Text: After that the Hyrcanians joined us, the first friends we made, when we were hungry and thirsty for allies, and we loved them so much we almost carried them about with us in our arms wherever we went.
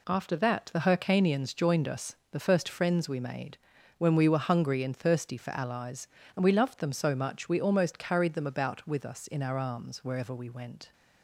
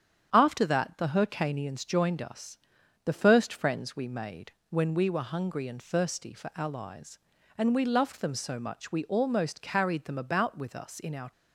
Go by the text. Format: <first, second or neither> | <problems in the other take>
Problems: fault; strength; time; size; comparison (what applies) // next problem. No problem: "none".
first | starts louder than the rest; strong; until 1.3 s; 8.5 dB // stops before "arms wherever we went"; at 11.3 s